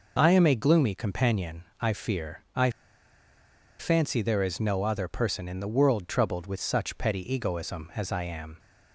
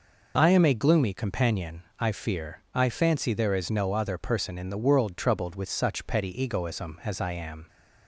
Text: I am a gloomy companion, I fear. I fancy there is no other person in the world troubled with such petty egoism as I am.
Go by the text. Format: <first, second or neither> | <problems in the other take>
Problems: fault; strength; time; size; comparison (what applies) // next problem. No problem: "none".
second | pauses between "I" and "fancy"; at 2.7 s; 1.0 s long